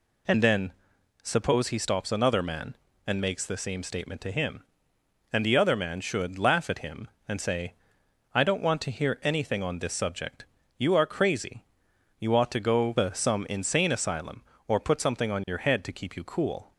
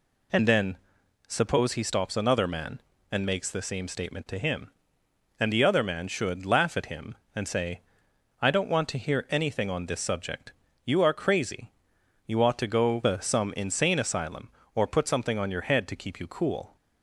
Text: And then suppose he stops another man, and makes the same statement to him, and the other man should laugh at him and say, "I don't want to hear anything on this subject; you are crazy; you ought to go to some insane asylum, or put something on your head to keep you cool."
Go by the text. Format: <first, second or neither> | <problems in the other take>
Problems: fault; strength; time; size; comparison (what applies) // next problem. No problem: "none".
neither | pauses between "then" and "suppose"; noticeable; the same in both